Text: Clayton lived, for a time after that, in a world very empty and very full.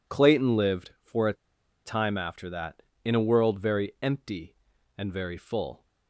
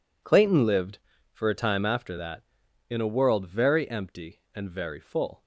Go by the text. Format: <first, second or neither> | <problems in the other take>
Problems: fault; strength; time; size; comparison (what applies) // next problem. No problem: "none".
second | pauses between "a" and "time"; noticeable; at 1.3 s; 0.52 s long